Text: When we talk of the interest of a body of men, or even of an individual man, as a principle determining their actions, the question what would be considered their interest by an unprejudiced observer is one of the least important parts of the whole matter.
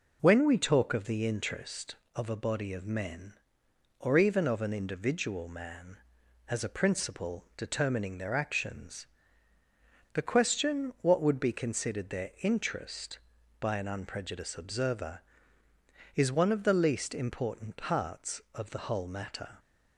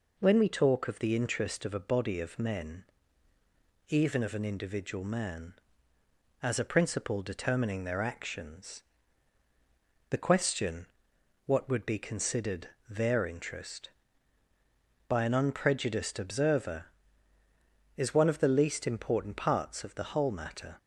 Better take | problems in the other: first | skips "or"; at 3.3 s // pauses between "question" and "what"; noticeable; at 10.8 s; 0.58 s long // pauses between "considered" and "their"; slight; at 12.6 s; 0.20 s long

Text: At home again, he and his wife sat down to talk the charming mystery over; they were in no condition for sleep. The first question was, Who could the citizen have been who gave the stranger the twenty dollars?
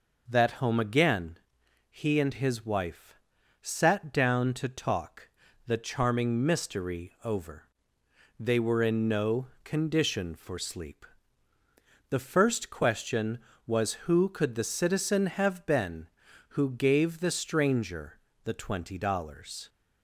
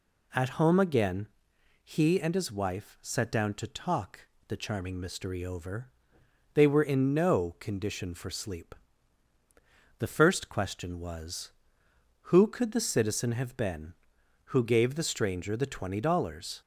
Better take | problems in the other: second | says "That" for "At"; at 0.2 s // pauses between "wife" and "sat"; noticeable; at 3.1 s; 0.46 s long // pauses between "talk" and "the"; at 5.2 s; 0.38 s long; slight in the second // pauses between "no" and "condition"; slight; at 9.4 s; 0.16 s long // pauses between "stranger" and "the"; slight; at 18.1 s; 0.24 s long

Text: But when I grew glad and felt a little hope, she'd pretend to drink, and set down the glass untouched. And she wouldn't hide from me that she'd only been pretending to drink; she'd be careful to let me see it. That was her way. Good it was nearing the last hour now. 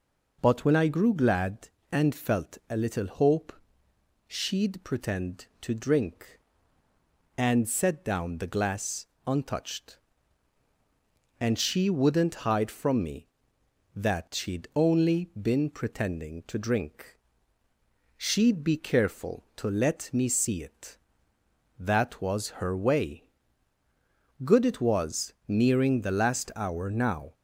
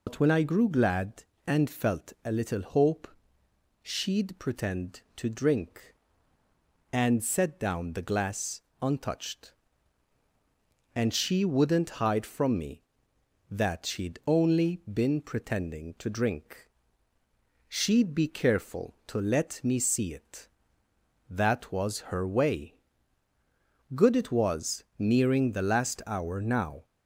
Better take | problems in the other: first | loses the start of "But"; at 0.0 s; 115 ms // pauses between "glass" and "untouched"; slight; at 8.6 s; 0.20 s long; slight in the first

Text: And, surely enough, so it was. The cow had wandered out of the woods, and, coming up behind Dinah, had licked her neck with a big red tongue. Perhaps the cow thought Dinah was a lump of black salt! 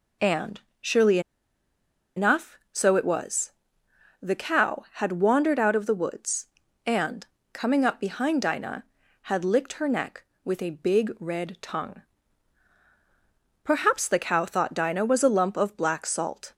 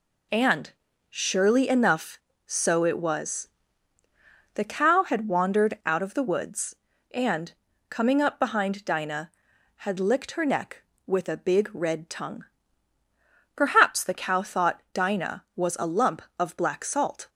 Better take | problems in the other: second | pauses between "surely" and "enough"; noticeable; at 1.1 s; 0.96 s long

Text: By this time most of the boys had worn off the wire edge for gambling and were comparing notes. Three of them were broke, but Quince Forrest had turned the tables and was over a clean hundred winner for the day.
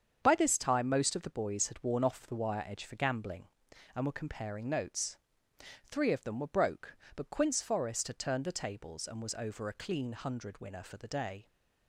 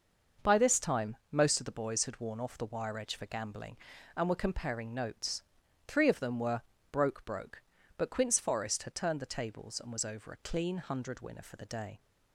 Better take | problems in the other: first | starts louder than the rest; until 1.5 s; 6 dB; strong in the first // pauses between "were" and "broke"; slight; at 6.6 s; 0.30 s long // says "broke" twice; at 7.2 s

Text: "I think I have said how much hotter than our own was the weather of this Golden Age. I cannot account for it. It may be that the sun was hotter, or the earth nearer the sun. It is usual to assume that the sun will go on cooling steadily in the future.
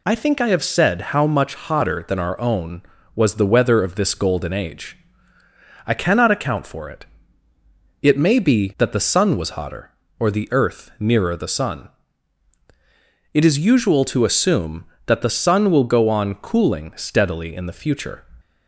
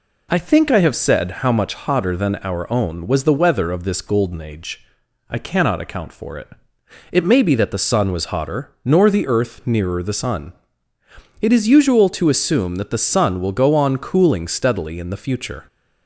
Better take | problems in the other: first | says "nor" for "or"; at 8.8 s

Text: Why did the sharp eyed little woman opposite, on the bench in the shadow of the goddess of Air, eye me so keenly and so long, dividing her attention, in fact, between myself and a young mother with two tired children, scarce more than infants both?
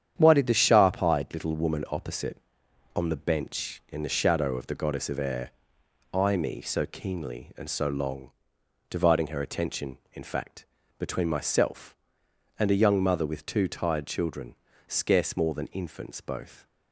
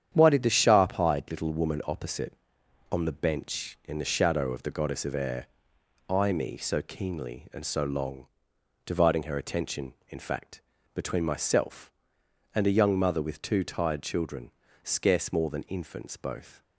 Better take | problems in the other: neither | starts louder than the rest; strong; the same in both

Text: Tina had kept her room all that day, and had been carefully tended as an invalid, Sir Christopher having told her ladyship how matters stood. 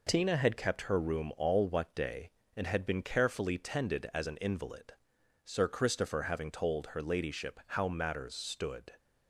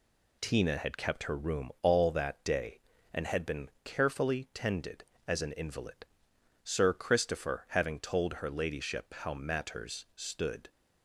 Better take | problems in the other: second | says "what" for "that"; at 1.6 s

